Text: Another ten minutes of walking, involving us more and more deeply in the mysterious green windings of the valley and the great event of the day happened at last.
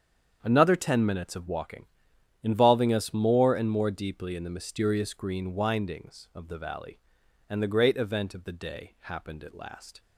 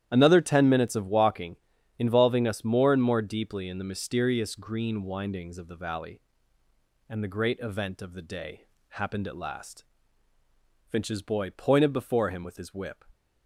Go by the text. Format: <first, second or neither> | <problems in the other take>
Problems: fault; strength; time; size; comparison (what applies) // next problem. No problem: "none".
first | starts louder than the rest; strong; until 1.1 s; 11 dB; strong in the first // pauses between "day" and "happened"; slight; at 8.6 s; 0.26 s long // goes on to say "Finch's boy pointed before him with his whip"; strong; from 10.8 s on; 2.1 s long